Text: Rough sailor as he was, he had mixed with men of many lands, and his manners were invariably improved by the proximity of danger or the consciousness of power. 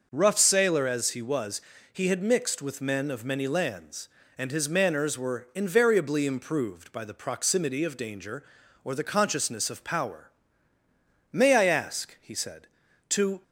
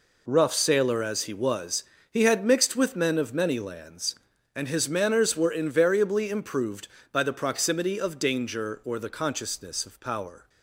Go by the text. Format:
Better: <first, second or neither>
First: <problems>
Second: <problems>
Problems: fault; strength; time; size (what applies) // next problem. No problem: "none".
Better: second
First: starts louder than the rest; noticeable; until 1.1 s; 6 dB // goes on to say "May I ask he said to"; strong; from 11.3 s on; 2.1 s long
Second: none